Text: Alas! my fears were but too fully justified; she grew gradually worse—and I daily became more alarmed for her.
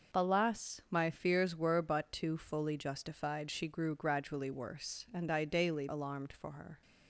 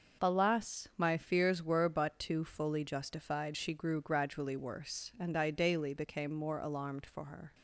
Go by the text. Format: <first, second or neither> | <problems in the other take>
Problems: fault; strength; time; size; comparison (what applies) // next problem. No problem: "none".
second | skips "became more"; at 5.8 s